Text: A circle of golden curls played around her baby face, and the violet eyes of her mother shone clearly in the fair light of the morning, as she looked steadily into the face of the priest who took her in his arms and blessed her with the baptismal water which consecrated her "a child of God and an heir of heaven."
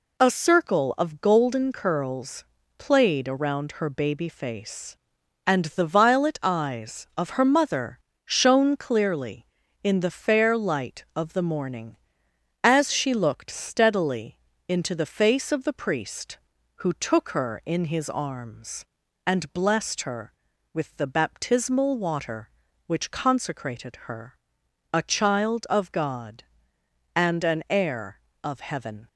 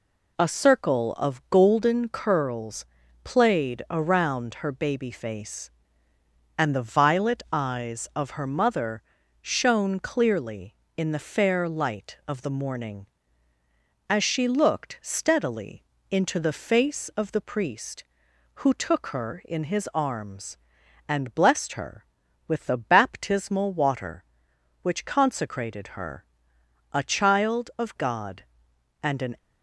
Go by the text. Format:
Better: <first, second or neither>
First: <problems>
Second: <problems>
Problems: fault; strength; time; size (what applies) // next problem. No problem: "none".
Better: first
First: pauses between "curls" and "played"; slight; at 2.4 s; 0.32 s long // pauses between "mother" and "shone"; slight; at 7.9 s; 0.24 s long // pauses between "steadily" and "into"; slight; at 14.3 s; 0.30 s long // pauses between "her" and "a"; noticeable; at 24.3 s; 0.56 s long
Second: pauses between "curls" and "played"; at 2.8 s; 0.38 s long // pauses between "mother" and "shone"; at 9.0 s; 0.40 s long // pauses between "steadily" and "into"; slight; at 15.8 s; 0.26 s long // pauses between "her" and "a"; noticeable; at 26.2 s; 0.68 s long // stops before "heir of heaven"; at 29.3 s